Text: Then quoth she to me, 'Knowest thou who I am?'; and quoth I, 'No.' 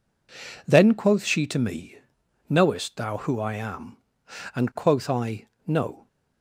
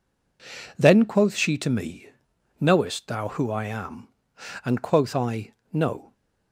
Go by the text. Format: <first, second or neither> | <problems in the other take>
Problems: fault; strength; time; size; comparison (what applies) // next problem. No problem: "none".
neither | none